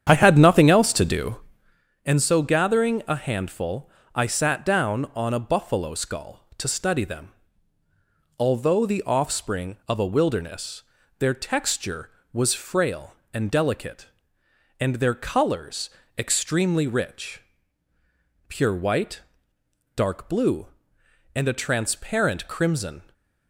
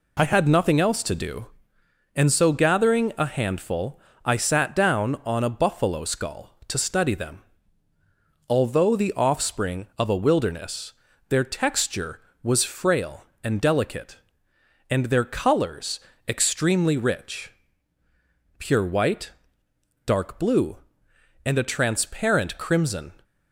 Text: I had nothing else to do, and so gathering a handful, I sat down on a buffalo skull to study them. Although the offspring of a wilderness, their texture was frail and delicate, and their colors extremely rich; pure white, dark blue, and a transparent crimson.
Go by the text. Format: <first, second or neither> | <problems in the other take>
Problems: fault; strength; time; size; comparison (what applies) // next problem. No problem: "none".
second | starts louder than the rest; strong; until 1.9 s; 8.5 dB // pauses between "colors" and "extremely"; slight; at 15.8 s; 0.26 s long; slight in the second